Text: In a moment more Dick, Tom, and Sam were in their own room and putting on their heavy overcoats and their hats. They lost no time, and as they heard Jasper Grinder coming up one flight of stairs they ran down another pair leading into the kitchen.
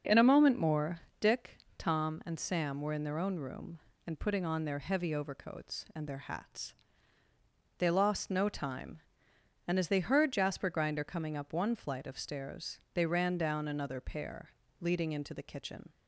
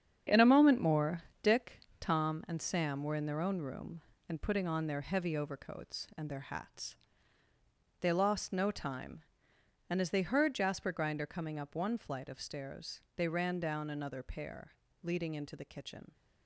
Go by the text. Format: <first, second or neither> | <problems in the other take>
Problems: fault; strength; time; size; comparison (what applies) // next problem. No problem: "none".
first | gets quieter; strong; throughout; 9 dB // starts louder than the rest; strong; until 1.4 s; 8 dB; also in the first // pauses between "more" and "Dick"; slight; at 1.2 s; 0.20 s long; slight in the first // pauses between "stairs" and "they"; slight; at 12.9 s; 0.16 s long; slight in the first // pauses between "pair" and "leading"; slight; at 14.7 s; 0.30 s long; slight in the first